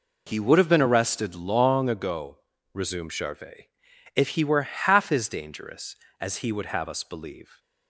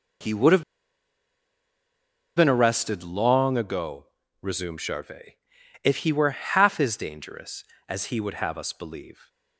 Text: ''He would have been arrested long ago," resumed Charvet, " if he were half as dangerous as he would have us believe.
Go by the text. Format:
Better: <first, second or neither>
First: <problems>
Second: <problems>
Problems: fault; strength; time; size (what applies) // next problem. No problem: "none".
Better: first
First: none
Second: pauses between "have" and "been"; strong; at 0.6 s; 1.7 s long